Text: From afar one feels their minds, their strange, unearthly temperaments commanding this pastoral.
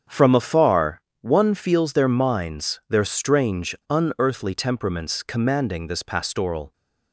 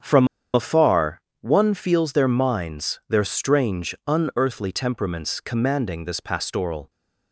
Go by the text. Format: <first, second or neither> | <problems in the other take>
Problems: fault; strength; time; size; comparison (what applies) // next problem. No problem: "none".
first | starts louder than the rest; strong; until 1.5 s; 7.5 dB; strong in the first // pauses between "From" and "afar"; slight; at 0.2 s; 0.26 s long // pauses between "afar" and "one"; slight; at 1.1 s; 0.22 s long; slight in the first